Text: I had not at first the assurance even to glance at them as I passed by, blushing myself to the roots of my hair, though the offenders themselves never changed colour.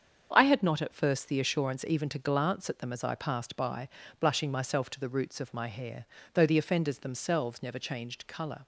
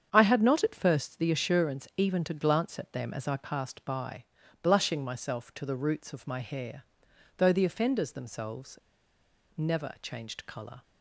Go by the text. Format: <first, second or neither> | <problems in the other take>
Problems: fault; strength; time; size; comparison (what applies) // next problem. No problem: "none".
first | starts louder than the rest; strong; until 1.1 s; 8 dB; strong in the first // pauses between "themselves" and "never"; noticeable; at 8.7 s; 0.77 s long